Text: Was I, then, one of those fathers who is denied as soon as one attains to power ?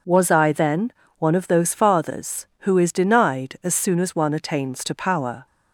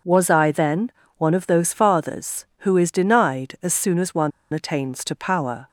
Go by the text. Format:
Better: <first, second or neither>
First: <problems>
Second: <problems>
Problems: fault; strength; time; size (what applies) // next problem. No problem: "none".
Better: first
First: none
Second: pauses between "one" and "attains"; slight; at 4.3 s; 0.23 s long